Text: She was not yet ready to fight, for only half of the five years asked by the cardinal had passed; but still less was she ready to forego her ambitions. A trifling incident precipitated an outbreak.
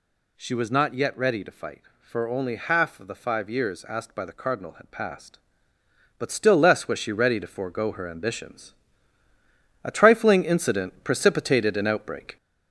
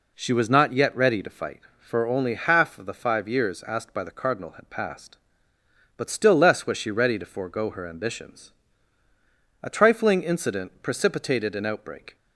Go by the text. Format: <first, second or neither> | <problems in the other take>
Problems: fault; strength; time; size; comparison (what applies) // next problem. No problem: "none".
second | gets louder; noticeable; throughout; 4 dB